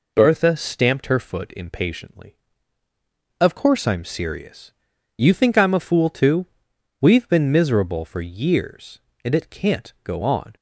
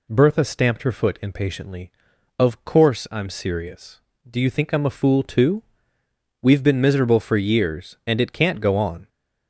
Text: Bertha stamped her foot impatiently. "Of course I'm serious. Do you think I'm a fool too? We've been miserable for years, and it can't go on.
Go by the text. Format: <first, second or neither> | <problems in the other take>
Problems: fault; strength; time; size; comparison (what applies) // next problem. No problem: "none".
second | skips "Do"; at 4.9 s